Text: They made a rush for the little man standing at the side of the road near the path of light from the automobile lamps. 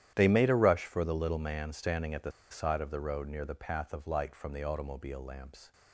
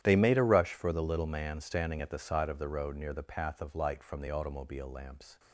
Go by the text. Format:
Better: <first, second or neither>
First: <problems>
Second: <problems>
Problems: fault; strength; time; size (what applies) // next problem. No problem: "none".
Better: second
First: starts louder than the rest; strong; until 1.1 s; 11 dB // pauses between "the" and "side"; slight; at 2.3 s; 0.20 s long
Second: starts louder than the rest; strong; until 1.0 s; 11 dB